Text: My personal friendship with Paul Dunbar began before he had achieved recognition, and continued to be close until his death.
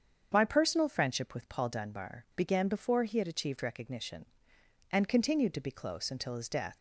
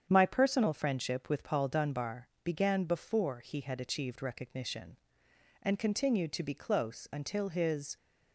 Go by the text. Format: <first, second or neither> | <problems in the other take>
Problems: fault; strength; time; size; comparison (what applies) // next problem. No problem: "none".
first | starts louder than the rest; strong; until 1.1 s; 8 dB; strong in the first // pauses between "Dunbar" and "began"; slight; at 2.2 s; 0.16 s long // stops before "death"; at 7.9 s